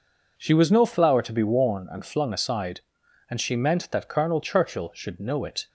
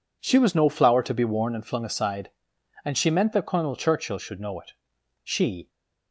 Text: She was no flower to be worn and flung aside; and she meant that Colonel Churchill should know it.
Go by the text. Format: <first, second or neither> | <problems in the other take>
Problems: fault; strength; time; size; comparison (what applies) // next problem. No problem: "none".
first | goes on to say "She"; slight; from 5.2 s on; 0.46 s long